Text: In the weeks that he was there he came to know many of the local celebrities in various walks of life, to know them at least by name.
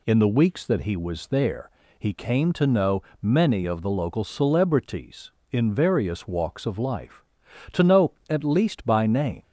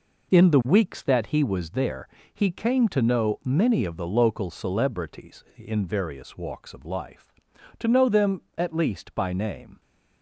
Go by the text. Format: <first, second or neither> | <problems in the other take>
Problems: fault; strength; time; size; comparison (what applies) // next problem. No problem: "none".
second | pauses between "there" and "he"; slight; at 1.6 s; 0.28 s long; slight in the second // pauses between "know" and "many"; slight; at 3.0 s; 0.20 s long // skips "them"; at 8.2 s